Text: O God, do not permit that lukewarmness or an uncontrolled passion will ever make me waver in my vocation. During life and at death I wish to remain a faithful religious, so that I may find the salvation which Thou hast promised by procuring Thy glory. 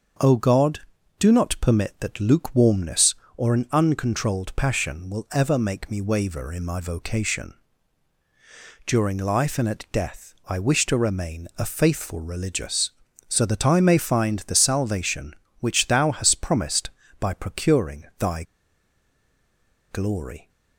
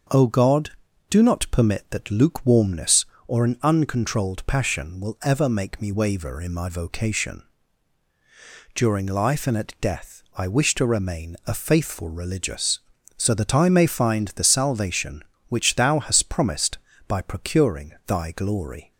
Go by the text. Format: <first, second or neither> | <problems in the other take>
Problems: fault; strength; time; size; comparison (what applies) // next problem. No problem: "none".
second | starts louder than the rest; until 1.6 s; 6.5 dB; also in the second // pauses between "Thy" and "glory"; strong; at 18.4 s; 1.4 s long